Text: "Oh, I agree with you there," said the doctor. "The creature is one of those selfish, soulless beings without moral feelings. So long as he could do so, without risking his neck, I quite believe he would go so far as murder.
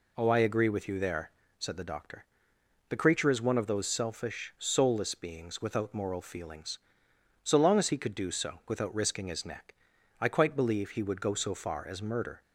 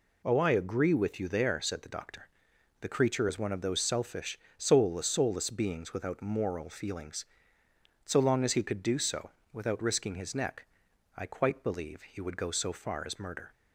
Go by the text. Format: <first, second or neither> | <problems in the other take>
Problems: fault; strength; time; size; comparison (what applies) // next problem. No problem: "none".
first | says "soulless" twice; at 5.0 s